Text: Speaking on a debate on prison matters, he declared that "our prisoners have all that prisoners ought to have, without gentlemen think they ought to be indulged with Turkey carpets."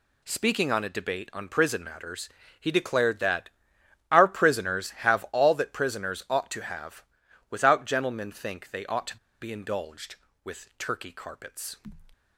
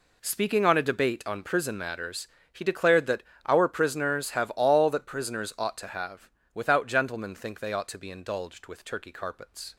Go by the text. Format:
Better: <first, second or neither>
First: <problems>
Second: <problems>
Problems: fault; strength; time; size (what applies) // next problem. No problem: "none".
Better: second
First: pauses between "that" and "our"; noticeable; at 3.4 s; 0.60 s long // pauses between "to" and "be"; slight; at 9.1 s; 0.24 s long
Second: pauses between "that" and "our"; slight; at 3.2 s; 0.24 s long